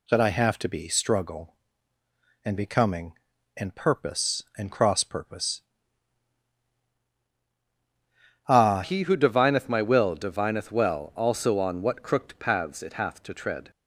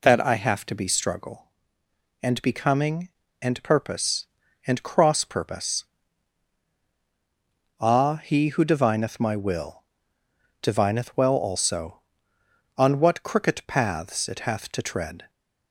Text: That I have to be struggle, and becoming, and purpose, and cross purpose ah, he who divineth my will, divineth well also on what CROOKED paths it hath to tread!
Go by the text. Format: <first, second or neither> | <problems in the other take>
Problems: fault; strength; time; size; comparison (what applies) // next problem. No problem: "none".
second | pauses between "purpose" and "ah"; strong; at 5.6 s; 2.8 s long; strong in the second // changes voice at "he"; from 8.8 s on; 4.9 s long